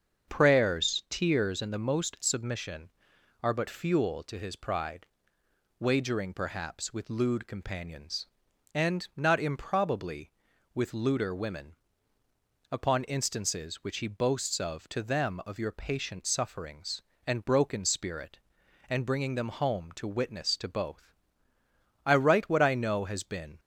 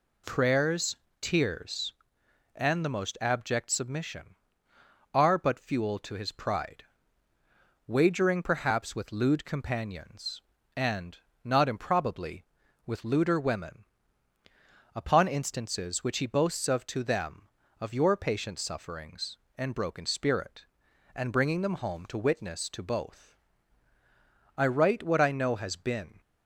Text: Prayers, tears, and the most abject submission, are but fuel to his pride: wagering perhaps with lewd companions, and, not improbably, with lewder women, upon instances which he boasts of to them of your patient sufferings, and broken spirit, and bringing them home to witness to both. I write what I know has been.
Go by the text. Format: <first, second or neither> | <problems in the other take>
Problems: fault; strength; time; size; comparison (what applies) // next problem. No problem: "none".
second | starts louder than the rest; until 1.3 s; 7 dB // skips "abject"; at 2.1 s